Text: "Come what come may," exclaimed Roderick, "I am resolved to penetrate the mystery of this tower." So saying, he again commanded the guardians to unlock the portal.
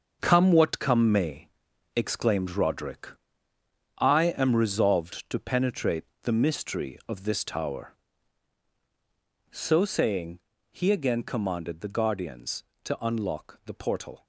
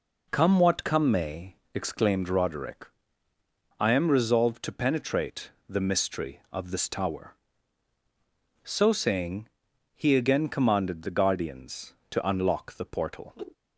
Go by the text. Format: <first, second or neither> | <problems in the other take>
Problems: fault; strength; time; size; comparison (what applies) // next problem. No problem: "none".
second | gets quieter; strong; throughout; 10.5 dB // pauses between "penetrate" and "the"; slight; at 6.0 s; 0.20 s long; slight in the second